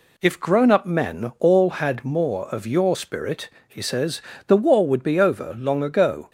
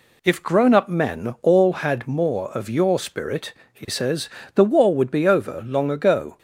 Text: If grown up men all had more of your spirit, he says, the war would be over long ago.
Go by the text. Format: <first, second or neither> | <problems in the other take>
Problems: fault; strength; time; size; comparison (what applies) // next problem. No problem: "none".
neither | none